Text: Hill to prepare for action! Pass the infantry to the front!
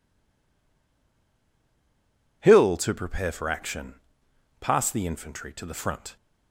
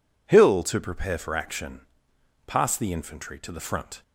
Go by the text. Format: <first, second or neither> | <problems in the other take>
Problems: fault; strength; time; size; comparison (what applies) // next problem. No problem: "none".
second | stays silent before the first word; until 2.4 s; 2.4 s long